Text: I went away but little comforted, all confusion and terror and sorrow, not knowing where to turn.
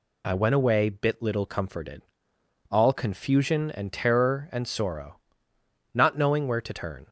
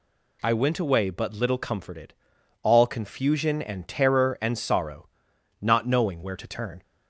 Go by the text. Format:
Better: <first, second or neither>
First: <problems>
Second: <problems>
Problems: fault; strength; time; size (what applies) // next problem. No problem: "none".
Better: second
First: says "bit" for "but"; at 0.8 s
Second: none